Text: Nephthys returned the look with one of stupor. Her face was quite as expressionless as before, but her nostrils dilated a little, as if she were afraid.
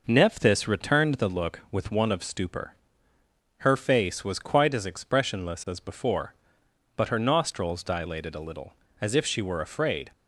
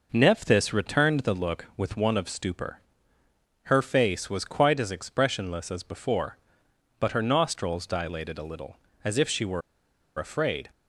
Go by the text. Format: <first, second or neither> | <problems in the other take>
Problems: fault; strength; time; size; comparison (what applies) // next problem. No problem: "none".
first | pauses between "were" and "afraid"; noticeable; at 9.6 s; 0.56 s long